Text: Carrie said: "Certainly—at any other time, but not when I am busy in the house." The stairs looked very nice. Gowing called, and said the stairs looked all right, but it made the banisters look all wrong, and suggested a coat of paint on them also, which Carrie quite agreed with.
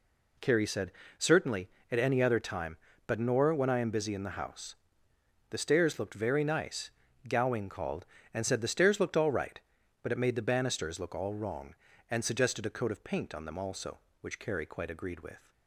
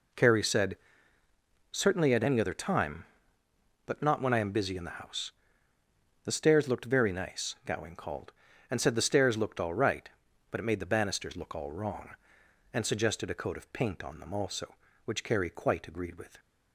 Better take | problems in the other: second | says "nor" for "not"; at 3.1 s

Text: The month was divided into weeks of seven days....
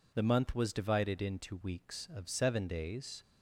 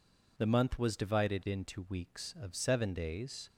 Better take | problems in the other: neither | none

